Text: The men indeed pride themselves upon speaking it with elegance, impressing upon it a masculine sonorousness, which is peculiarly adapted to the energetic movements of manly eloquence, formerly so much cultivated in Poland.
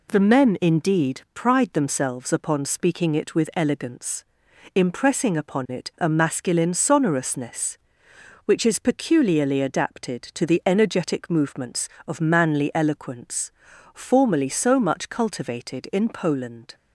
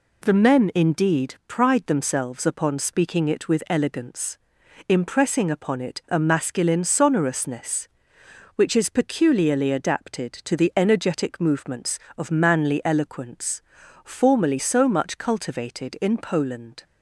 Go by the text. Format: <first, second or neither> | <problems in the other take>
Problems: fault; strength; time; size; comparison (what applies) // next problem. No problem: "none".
neither | none